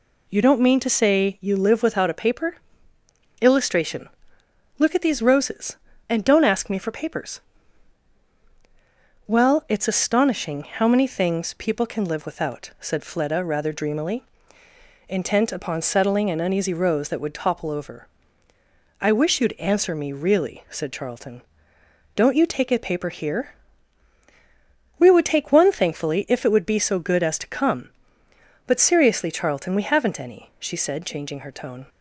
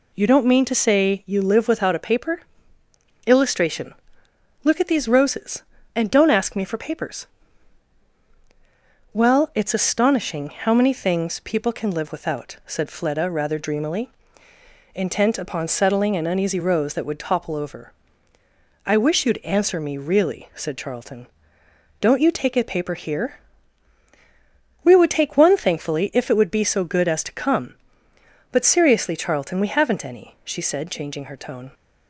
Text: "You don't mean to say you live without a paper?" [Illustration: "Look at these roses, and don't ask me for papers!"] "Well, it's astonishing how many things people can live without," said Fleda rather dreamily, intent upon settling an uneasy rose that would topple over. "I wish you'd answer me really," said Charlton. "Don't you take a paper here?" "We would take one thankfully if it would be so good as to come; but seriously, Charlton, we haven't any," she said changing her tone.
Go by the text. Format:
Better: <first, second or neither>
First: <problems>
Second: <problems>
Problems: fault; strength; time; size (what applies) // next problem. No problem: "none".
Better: neither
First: none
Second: none